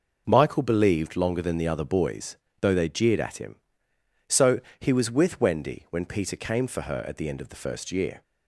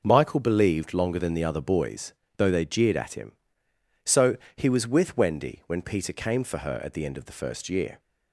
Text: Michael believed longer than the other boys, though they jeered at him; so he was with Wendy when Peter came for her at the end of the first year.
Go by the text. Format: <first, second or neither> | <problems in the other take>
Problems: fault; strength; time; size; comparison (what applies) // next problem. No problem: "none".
neither | pauses between "so" and "he"; slight; the same in both